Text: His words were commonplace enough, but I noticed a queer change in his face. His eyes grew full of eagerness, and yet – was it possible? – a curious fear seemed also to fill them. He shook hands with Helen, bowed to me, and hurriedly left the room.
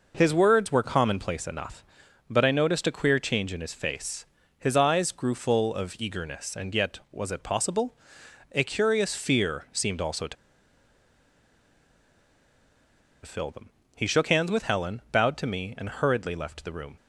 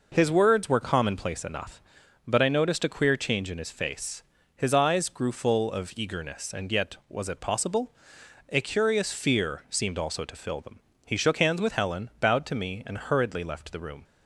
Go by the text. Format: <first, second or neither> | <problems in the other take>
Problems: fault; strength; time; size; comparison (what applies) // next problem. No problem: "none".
second | pauses between "to" and "fill"; strong; at 10.3 s; 2.8 s long